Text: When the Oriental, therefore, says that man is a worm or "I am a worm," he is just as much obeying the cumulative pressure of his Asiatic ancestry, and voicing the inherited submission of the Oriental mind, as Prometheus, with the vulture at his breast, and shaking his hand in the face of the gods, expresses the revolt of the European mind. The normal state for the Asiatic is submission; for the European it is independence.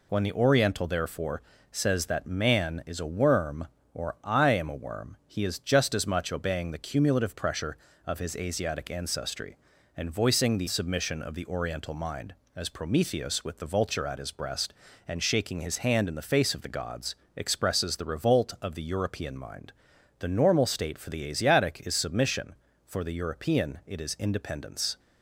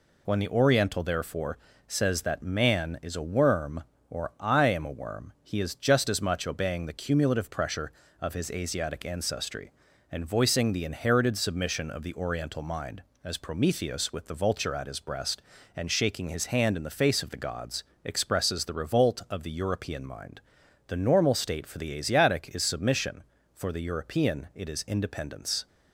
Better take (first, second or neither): second